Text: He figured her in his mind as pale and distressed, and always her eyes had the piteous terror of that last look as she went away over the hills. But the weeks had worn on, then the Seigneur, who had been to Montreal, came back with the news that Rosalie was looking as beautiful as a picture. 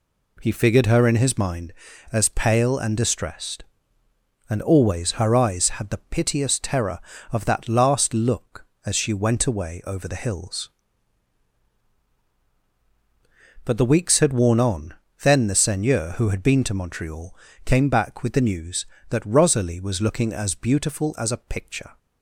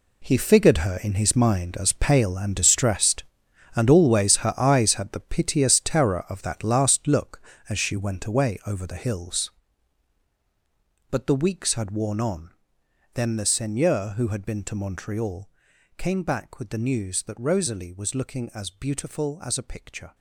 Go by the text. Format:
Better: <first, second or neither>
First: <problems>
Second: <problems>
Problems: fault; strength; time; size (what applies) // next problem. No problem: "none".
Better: first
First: none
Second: gets quieter; strong; throughout; 12 dB